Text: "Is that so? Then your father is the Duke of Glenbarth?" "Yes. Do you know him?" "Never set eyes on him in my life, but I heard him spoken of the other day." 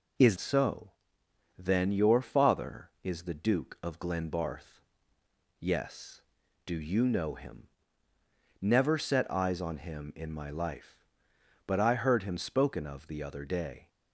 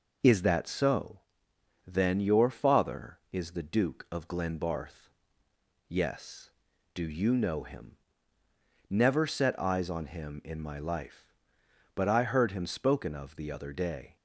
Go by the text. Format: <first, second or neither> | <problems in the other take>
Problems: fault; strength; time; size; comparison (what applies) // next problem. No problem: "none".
second | skips "that"; at 0.3 s